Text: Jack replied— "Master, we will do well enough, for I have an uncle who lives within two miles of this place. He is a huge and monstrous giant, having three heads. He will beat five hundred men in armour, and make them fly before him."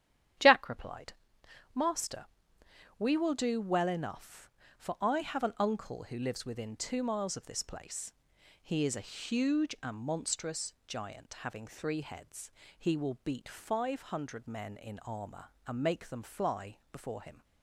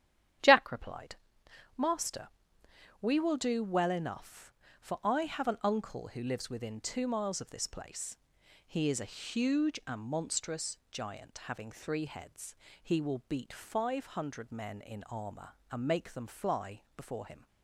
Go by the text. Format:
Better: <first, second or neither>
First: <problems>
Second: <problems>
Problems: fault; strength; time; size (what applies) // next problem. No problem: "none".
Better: neither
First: starts louder than the rest; strong; until 2.0 s; 10.5 dB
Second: starts louder than the rest; strong; until 2.0 s; 10.5 dB